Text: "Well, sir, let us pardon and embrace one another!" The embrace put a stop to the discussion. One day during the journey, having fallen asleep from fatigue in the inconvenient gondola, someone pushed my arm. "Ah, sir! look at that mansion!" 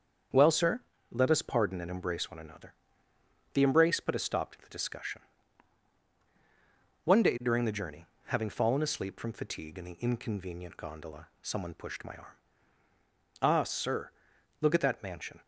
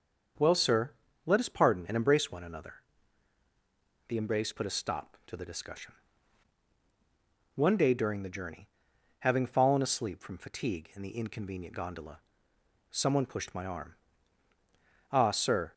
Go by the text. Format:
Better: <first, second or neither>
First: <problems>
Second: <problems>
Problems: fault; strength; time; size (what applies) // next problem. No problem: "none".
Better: first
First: starts louder than the rest; strong; until 1.6 s; 7 dB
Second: starts louder than the rest; until 1.7 s; 7 dB // stops before "look at that mansion"; at 15.7 s